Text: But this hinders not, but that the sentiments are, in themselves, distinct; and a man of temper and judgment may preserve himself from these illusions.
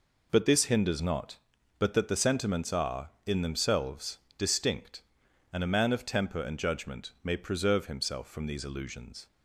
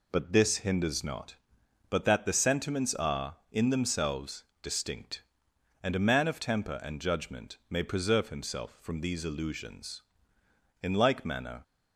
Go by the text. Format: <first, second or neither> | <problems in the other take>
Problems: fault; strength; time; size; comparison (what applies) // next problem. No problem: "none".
first | goes on to say "In like manner"; noticeable; from 10.8 s on; 0.80 s long